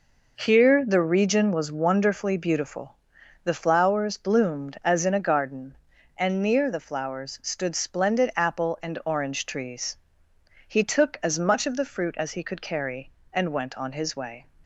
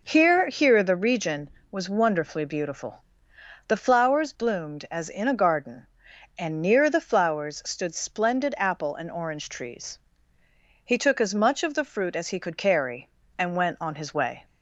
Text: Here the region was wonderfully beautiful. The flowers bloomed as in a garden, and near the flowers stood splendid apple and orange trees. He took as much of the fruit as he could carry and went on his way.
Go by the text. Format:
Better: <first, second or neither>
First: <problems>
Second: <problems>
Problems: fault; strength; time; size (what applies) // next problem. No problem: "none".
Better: first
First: none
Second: says "Here" twice; at 0.4 s